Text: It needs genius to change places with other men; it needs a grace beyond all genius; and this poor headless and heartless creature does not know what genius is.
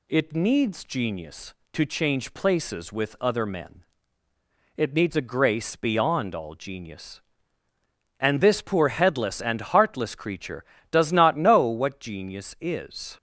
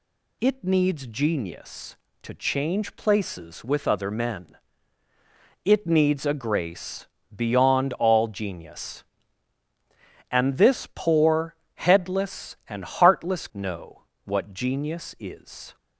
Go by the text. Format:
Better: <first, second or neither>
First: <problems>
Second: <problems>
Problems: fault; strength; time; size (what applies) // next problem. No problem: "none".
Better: first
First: none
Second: pauses between "grace" and "beyond"; slight; at 7.0 s; 0.26 s long // pauses between "poor" and "headless"; slight; at 11.5 s; 0.20 s long // skips "creature does not"; at 13.5 s // pauses between "know" and "what"; slight; at 14.0 s; 0.18 s long